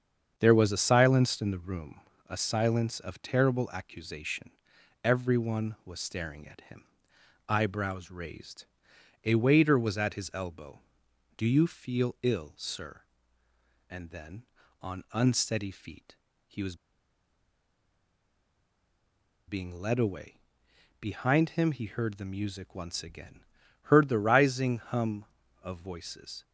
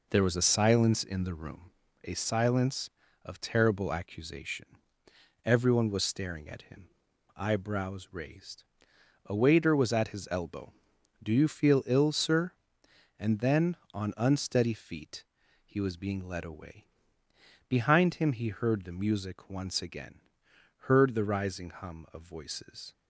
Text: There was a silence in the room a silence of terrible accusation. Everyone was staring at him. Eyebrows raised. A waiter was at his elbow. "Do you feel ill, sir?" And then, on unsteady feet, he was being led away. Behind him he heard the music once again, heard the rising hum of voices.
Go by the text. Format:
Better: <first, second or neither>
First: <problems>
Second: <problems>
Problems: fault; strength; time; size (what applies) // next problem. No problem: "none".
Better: second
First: starts louder than the rest; strong; until 1.3 s; 7.5 dB // pauses between "room" and "a"; slight; at 2.0 s; 0.28 s long // pauses between "was" and "being"; strong; at 16.7 s; 2.7 s long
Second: pauses between "room" and "a"; slight; at 1.7 s; 0.34 s long